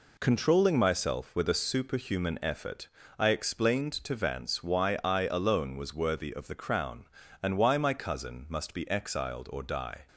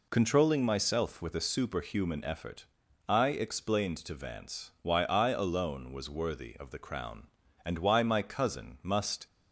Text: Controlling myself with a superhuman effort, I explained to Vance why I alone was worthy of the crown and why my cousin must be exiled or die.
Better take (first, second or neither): first